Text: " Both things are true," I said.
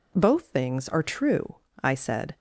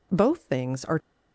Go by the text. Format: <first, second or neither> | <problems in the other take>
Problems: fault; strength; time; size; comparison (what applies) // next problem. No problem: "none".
first | stops before "true I said"; at 0.9 s